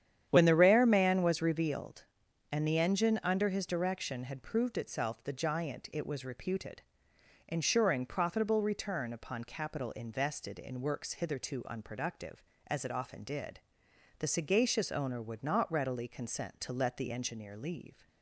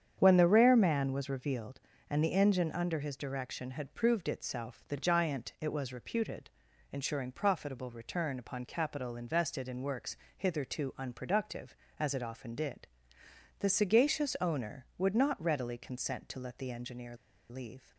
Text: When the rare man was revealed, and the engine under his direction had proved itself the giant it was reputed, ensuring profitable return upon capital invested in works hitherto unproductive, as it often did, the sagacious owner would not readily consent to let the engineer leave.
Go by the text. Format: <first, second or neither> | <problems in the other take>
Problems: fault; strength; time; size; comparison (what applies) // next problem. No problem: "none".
first | starts louder than the rest; strong; until 1.1 s; 8.5 dB; strong in the first // pauses between "works" and "hitherto"; slight; at 10.1 s; 0.20 s long // pauses between "engineer" and "leave"; slight; at 17.1 s; 0.34 s long